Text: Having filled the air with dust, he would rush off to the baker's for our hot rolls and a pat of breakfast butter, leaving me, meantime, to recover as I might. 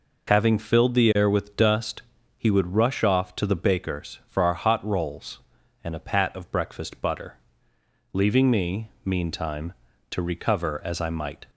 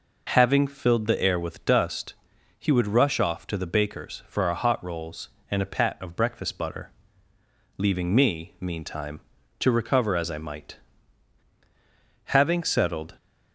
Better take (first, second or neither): first